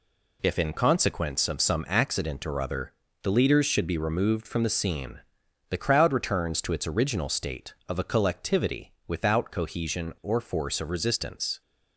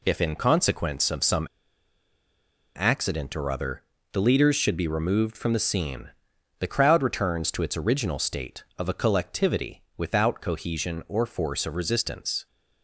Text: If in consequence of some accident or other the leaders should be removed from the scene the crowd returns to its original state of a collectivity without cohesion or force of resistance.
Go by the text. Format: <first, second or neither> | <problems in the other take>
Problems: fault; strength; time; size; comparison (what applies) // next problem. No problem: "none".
first | pauses between "some" and "accident"; strong; at 1.4 s; 1.2 s long // pauses between "other" and "the"; slight; at 3.8 s; 0.30 s long; slight in the first // pauses between "scene" and "the"; noticeable; at 6.0 s; 0.50 s long; noticeable in the first // pauses between "collectivity" and "without"; slight; at 9.8 s; 0.16 s long; slight in the first